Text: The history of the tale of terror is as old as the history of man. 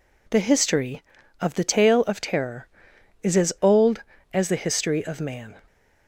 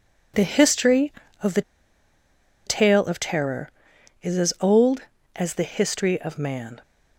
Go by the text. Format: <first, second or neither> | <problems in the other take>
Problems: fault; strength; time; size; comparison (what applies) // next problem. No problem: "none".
first | pauses between "the" and "tale"; at 1.6 s; 1.0 s long